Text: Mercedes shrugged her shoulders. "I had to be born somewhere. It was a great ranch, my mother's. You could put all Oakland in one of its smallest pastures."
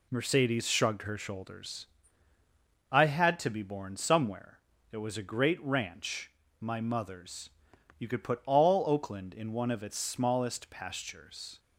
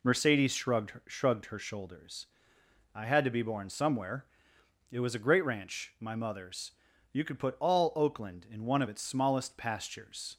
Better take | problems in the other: first | says "shrugged" twice; at 1.0 s

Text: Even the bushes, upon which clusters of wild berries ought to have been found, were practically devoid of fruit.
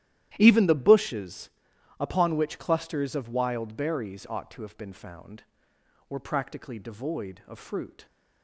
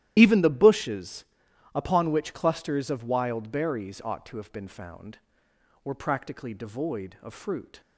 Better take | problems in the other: first | loses the start of "Even"; at 0.1 s; 85 ms // starts louder than the rest; strong; until 1.1 s; 13 dB; strong in the first

